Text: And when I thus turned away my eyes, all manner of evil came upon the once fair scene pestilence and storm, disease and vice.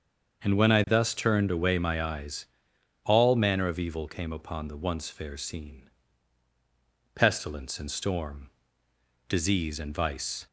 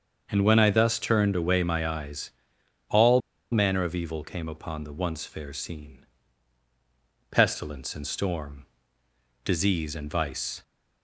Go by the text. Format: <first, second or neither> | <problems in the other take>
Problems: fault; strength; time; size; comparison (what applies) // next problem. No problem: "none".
first | starts louder than the rest; until 1.3 s; 6.5 dB; also in the first // pauses between "all" and "manner"; slight; at 3.1 s; 0.32 s long // pauses between "scene" and "pestilence"; strong; at 6.0 s; 1.3 s long; strong in the first